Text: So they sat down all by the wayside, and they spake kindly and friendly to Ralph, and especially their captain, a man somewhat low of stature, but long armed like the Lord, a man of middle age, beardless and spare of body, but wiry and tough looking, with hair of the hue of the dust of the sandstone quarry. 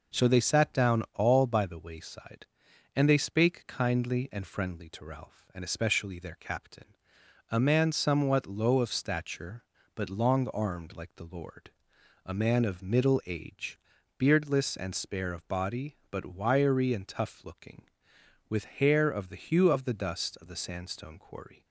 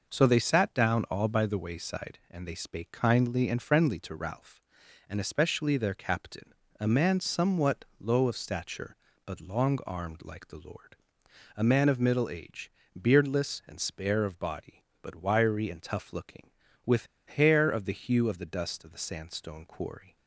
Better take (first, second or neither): first